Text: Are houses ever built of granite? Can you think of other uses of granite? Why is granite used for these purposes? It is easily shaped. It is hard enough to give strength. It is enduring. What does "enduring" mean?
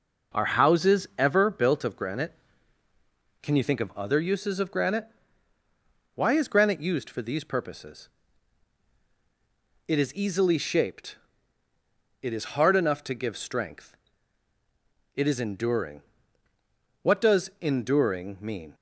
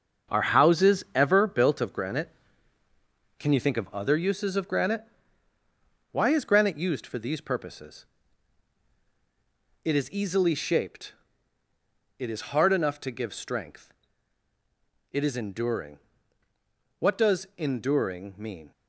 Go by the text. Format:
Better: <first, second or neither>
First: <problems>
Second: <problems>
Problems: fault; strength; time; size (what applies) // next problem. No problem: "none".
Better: first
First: none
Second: gets quieter; strong; throughout; 8.5 dB